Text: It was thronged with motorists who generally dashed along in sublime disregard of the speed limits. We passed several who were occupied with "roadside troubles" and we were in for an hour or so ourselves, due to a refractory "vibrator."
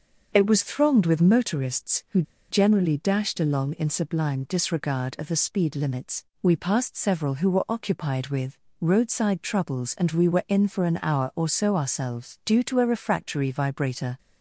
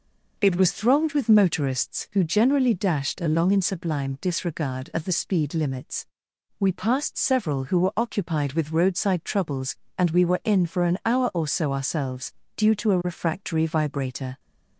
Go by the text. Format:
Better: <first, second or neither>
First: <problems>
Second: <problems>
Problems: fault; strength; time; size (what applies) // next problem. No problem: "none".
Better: second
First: starts louder than the rest; until 1.3 s; 6 dB // pauses between "who" and "generally"; slight; at 2.2 s; 0.27 s long // pauses between "with" and "roadside"; slight; at 8.5 s; 0.22 s long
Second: none